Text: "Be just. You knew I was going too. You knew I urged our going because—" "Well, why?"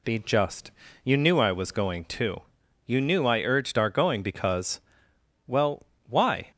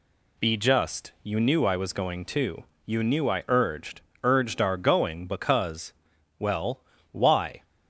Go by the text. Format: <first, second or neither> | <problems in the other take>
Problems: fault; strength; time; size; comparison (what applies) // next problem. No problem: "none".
first | says "urged" twice; at 4.2 s